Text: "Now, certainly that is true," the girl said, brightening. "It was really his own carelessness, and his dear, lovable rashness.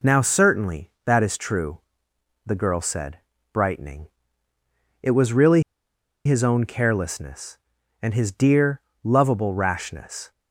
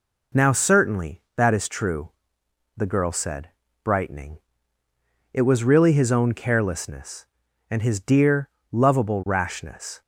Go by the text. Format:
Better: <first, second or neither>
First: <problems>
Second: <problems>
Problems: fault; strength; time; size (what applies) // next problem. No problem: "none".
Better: second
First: pauses between "really" and "his"; noticeable; at 5.6 s; 0.63 s long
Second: none